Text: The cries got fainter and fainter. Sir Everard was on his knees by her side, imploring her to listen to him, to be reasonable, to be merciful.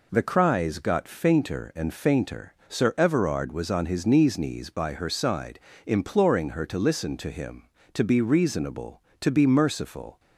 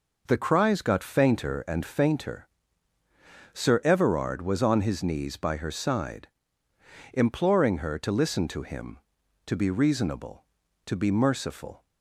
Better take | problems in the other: second | says "knees" twice; at 4.3 s

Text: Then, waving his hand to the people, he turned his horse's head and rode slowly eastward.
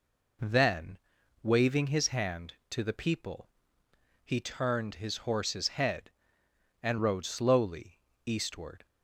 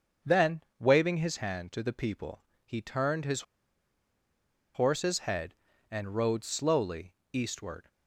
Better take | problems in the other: first | starts louder than the rest; until 1.4 s; 6.5 dB // pauses between "his" and "horse's"; strong; at 3.4 s; 1.3 s long // pauses between "slowly" and "eastward"; slight; at 7.1 s; 0.18 s long; slight in the first

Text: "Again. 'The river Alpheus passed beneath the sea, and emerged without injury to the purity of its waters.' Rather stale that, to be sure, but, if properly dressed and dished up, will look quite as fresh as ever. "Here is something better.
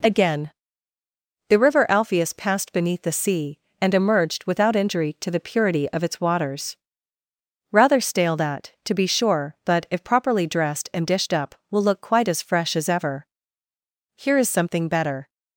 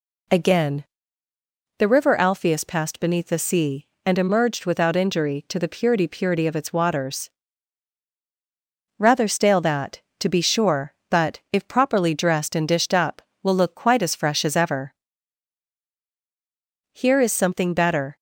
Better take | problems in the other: first | says "purity" twice; at 6.0 s

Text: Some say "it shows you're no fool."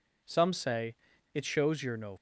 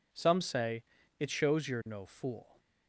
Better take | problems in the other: second | pauses between "say" and "it"; at 0.9 s; 0.38 s long; slight in the second // stops before "fool"; at 2.1 s

